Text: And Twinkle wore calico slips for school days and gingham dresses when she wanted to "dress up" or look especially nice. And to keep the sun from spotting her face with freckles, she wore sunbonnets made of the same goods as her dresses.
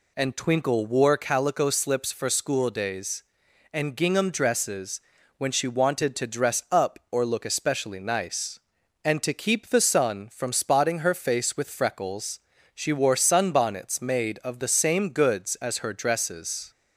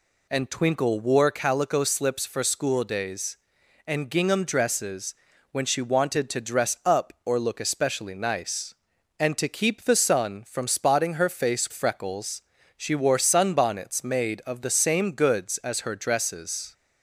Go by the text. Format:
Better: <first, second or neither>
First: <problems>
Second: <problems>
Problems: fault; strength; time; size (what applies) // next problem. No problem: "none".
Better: first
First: pauses between "dresses" and "when"; at 4.9 s; 0.38 s long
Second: pauses between "dresses" and "when"; at 5.1 s; 0.38 s long // skips "with"; at 11.7 s